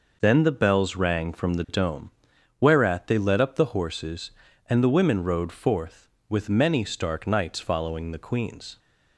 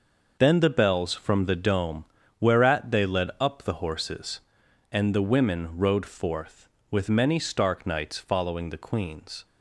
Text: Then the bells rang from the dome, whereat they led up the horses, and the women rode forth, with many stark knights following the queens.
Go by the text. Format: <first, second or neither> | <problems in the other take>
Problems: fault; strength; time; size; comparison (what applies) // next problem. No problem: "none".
first | skips "rang"; at 1.1 s